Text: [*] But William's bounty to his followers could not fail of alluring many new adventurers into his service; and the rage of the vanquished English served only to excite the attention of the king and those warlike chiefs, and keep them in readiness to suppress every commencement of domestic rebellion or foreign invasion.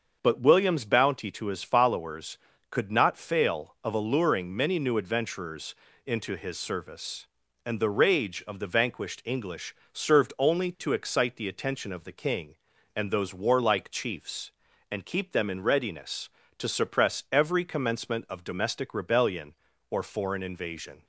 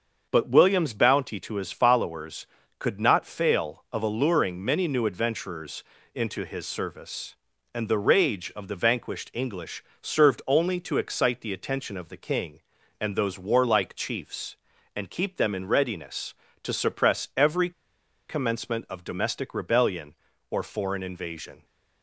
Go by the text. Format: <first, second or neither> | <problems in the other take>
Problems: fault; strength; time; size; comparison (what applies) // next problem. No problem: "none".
first | starts louder than the rest; until 1.2 s; 6.5 dB; also in the first // pauses between "adventurers" and "into"; slight; at 5.8 s; 0.30 s long; slight in the first // pauses between "English" and "served"; slight; at 9.8 s; 0.20 s long; slight in the first // pauses between "every" and "commencement"; noticeable; at 17.7 s; 0.57 s long